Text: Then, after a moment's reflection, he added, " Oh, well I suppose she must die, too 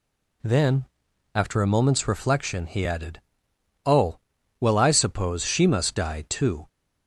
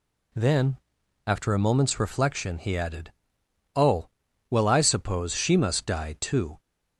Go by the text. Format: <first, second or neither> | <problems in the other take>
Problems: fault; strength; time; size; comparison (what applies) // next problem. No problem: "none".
neither | none